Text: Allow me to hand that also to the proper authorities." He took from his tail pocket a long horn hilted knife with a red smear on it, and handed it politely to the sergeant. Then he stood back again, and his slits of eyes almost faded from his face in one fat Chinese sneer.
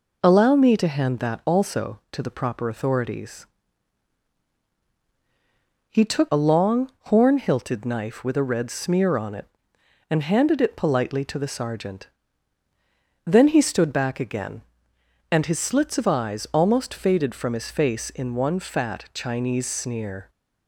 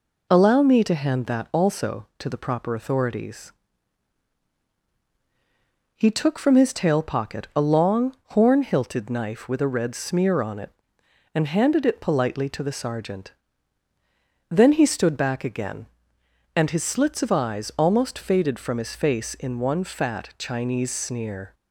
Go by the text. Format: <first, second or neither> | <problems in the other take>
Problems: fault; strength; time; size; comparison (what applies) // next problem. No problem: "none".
second | skips "from his tail pocket"; at 6.2 s